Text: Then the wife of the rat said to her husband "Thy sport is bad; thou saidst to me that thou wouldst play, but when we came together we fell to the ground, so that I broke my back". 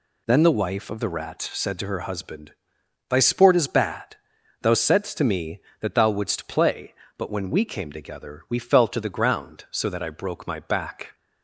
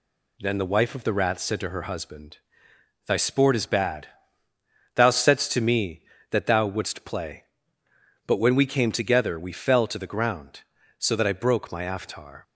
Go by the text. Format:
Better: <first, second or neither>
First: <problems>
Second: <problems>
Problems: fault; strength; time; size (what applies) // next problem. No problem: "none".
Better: first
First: pauses between "husband" and "Thy"; noticeable; at 2.5 s; 0.58 s long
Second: pauses between "husband" and "Thy"; noticeable; at 2.3 s; 0.70 s long // says "aftar" for "back"; at 11.8 s